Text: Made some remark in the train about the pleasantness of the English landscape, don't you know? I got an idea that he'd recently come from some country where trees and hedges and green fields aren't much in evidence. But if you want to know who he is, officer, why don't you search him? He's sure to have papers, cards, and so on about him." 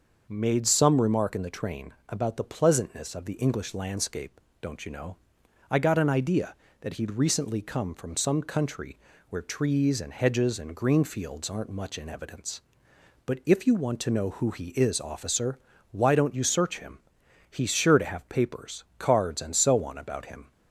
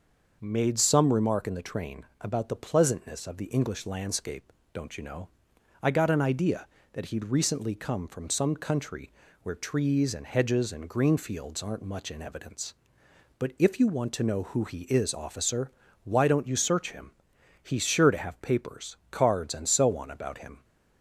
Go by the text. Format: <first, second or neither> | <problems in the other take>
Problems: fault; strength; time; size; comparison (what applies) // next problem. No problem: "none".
neither | starts louder than the rest; the same in both // pauses between "country" and "where"; slight; the same in both